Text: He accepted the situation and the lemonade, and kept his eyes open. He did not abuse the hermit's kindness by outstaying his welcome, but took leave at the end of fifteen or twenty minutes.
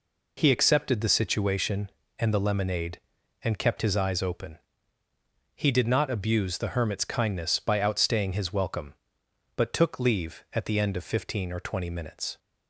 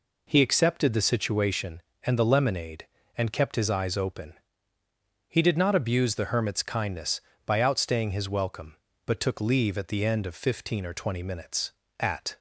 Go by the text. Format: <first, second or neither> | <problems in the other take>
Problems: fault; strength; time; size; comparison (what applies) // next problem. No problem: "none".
first | goes on to say "At"; slight; from 11.9 s on; 0.40 s long